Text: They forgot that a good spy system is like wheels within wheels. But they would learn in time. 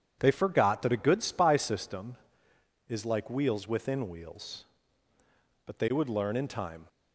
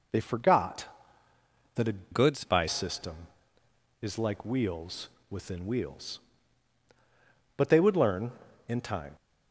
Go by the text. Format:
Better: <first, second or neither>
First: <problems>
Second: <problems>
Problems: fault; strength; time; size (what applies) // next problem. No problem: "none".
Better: first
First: none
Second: changes voice from "good" to "spy"; from 2.1 to 2.6 s; 0.5 s long // pauses between "wheels" and "within"; slight; at 5.0 s; 0.20 s long